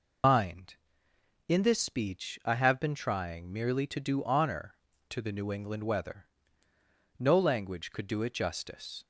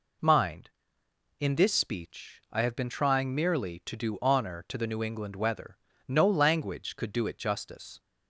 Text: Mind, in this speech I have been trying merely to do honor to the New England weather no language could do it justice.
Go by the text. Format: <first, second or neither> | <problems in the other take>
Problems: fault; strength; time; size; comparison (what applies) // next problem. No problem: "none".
second | loses the start of "Mind"; at 0.2 s; 110 ms // pauses between "weather" and "no"; noticeable; at 6.2 s; 0.92 s long; slight in the second